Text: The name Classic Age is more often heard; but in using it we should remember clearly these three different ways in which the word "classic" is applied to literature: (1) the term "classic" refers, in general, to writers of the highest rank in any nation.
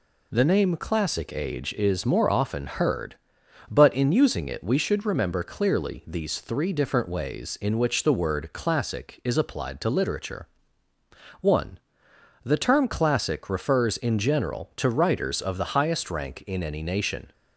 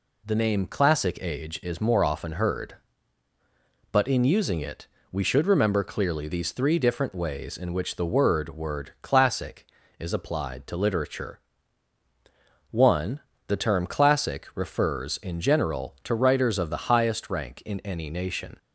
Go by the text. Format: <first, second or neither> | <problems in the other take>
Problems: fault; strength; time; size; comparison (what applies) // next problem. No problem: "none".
first | pauses between "it" and "we"; slight; at 4.8 s; 0.24 s long // says "word" twice; at 8.4 s